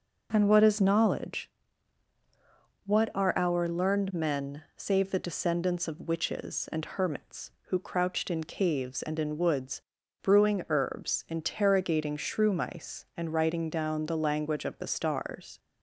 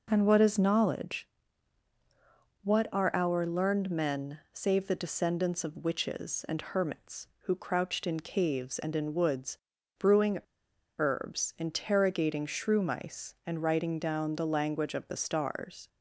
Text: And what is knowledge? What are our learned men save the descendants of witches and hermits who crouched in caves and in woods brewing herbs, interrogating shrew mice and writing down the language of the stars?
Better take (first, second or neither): first